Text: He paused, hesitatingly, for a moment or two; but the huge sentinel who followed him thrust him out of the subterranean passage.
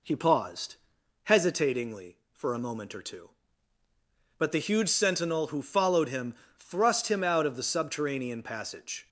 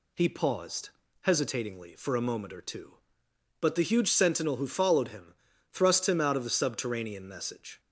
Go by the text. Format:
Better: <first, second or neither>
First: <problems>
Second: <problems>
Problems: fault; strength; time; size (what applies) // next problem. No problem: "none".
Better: first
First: pauses between "him" and "thrust"; slight; at 6.3 s; 0.24 s long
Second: pauses between "him" and "thrust"; at 5.3 s; 0.38 s long // says "message" for "passage"; at 7.2 s